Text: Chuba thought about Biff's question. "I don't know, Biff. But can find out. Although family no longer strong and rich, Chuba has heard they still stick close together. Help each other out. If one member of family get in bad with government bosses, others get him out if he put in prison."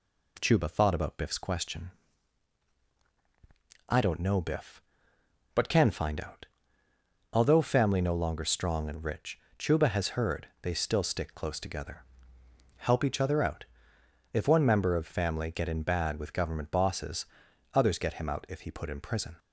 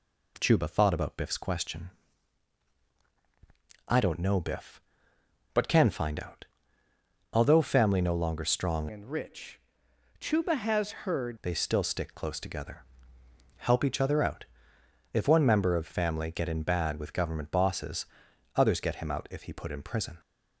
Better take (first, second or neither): first